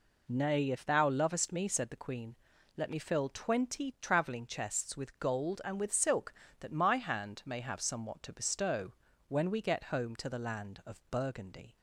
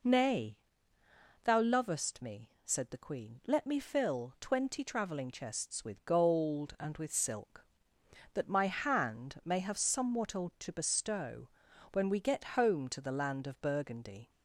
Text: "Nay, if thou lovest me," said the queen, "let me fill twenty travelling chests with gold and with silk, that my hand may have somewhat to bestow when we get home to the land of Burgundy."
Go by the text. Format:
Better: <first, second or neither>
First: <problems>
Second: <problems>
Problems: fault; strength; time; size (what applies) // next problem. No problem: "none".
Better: first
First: pauses between "bestow" and "when"; slight; at 8.9 s; 0.34 s long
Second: skips "if"; at 0.9 s // pauses between "bestow" and "when"; at 11.4 s; 0.42 s long